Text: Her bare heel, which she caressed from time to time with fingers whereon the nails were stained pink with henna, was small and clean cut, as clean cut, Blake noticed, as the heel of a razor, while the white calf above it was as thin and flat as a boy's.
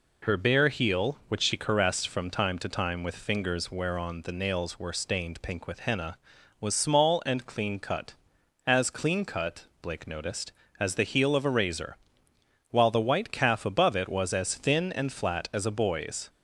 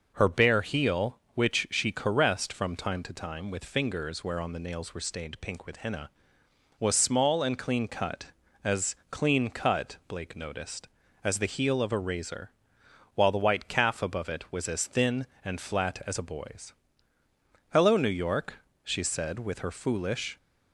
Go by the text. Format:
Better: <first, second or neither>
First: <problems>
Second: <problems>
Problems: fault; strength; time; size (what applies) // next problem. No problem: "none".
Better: first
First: none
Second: goes on to say "Hello New York she said with her foolish"; strong; from 17.7 s on; 2.6 s long